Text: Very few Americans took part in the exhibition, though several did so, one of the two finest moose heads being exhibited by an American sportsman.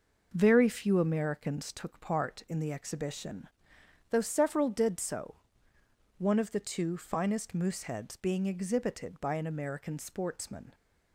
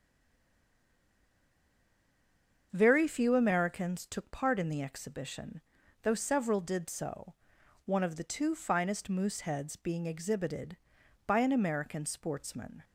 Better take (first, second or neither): first